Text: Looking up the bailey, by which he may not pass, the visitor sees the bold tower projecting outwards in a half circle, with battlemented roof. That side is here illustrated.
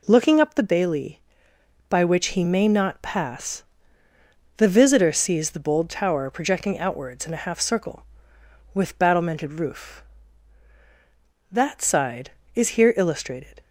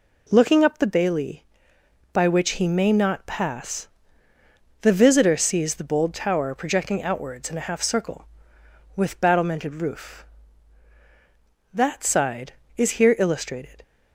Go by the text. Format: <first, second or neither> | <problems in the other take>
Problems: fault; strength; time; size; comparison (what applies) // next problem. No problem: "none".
neither | none